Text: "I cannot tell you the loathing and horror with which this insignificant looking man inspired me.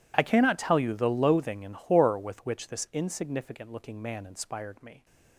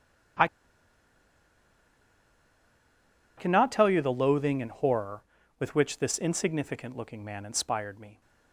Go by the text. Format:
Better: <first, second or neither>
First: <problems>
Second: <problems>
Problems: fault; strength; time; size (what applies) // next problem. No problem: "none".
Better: first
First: none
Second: pauses between "I" and "cannot"; strong; at 0.4 s; 2.9 s long